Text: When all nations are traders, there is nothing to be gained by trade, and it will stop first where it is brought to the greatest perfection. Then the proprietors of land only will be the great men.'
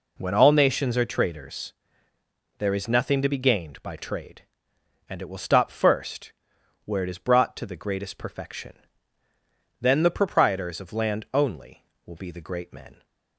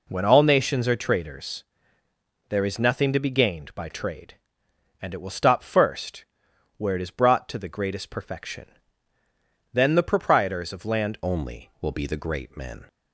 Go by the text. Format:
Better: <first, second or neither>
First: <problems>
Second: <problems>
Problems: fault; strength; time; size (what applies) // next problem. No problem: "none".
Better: first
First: pauses between "first" and "where"; noticeable; at 6.3 s; 0.54 s long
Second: pauses between "first" and "where"; noticeable; at 6.2 s; 0.54 s long // changes voice at "only"; from 11.2 s on; 1.6 s long